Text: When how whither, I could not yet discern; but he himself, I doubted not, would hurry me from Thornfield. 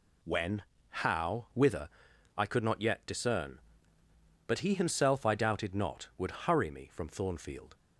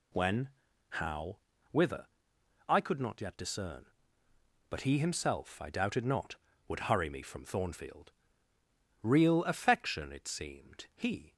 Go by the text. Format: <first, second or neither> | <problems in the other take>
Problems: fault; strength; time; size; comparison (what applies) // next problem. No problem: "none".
first | pauses between "When" and "how"; noticeable; at 0.4 s; 0.52 s long; slight in the first // pauses between "how" and "whither"; slight; at 1.3 s; 0.32 s long // goes on to say "Real affection it seemed he"; strong; from 9.0 s on; 2.3 s long